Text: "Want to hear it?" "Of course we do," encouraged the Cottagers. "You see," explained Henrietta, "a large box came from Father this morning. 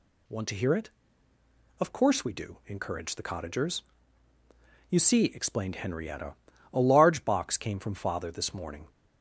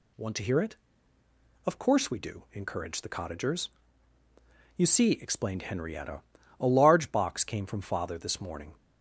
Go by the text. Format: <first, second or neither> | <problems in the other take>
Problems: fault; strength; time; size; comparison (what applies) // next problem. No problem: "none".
neither | none